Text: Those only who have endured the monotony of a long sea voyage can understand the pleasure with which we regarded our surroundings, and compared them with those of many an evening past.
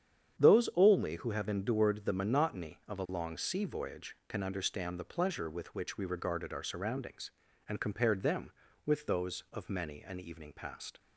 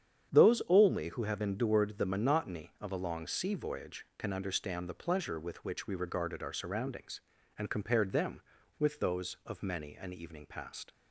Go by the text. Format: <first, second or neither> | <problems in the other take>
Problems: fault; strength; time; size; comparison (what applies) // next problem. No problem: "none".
neither | starts louder than the rest; strong; the same in both